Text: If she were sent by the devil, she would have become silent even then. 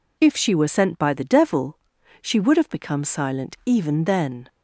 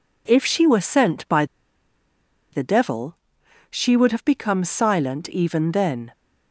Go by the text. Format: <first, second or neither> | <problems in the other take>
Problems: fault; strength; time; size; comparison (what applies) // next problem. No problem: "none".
first | pauses between "by" and "the"; at 1.4 s; 1.0 s long